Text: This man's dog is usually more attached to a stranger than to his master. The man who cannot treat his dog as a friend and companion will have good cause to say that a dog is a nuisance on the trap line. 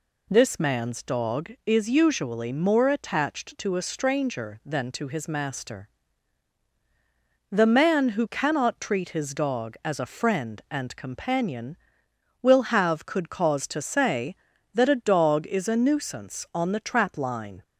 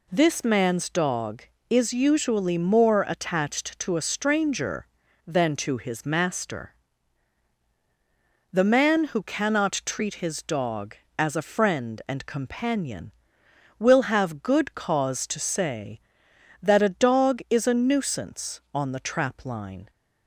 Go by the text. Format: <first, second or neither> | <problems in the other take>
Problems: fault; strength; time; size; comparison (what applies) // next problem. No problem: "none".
second | says "could" for "good"; at 13.0 s